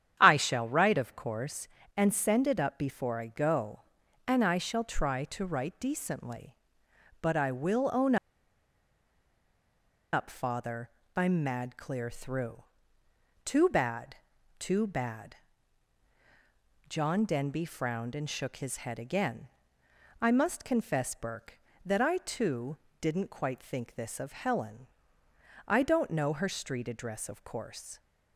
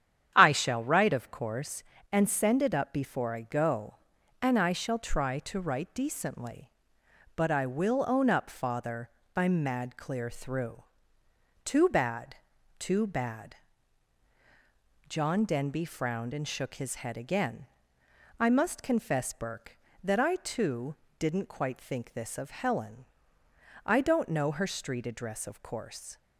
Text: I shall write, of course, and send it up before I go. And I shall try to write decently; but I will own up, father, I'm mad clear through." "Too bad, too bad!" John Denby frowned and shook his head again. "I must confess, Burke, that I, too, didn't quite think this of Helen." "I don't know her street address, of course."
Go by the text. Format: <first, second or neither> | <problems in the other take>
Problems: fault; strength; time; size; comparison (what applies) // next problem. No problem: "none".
second | starts louder than the rest; strong; until 1.2 s; 9.5 dB; strong in the second // pauses between "own" and "up"; strong; at 8.1 s; 1.9 s long